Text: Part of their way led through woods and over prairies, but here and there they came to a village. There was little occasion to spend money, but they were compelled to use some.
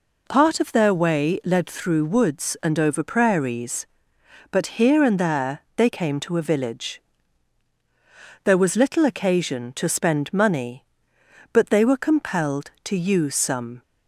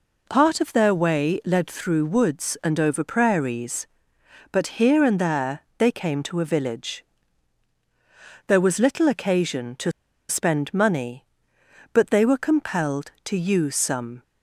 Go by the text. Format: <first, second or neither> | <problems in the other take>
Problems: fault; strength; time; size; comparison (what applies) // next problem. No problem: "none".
first | pauses between "there" and "they"; slight; at 5.6 s; 0.18 s long; slight in the first // pauses between "to" and "spend"; at 9.9 s; 0.39 s long